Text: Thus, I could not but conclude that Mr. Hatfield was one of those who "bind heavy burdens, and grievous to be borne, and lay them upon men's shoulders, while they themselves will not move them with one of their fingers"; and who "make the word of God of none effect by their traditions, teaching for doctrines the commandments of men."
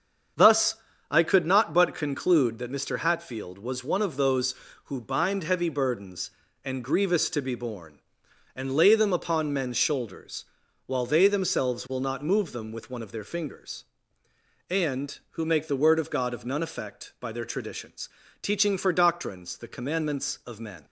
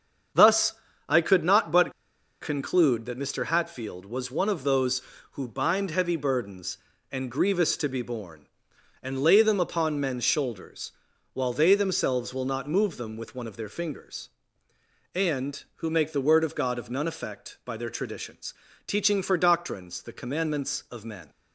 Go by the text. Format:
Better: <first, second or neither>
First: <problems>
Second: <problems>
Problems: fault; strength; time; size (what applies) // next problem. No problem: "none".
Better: first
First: starts louder than the rest; strong; until 1.7 s; 7 dB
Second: starts louder than the rest; strong; until 1.7 s; 7 dB // pauses between "but" and "conclude"; noticeable; at 1.9 s; 0.49 s long